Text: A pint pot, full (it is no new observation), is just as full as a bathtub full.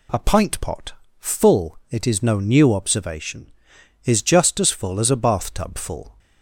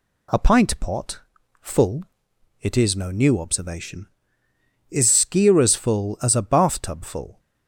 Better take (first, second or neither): first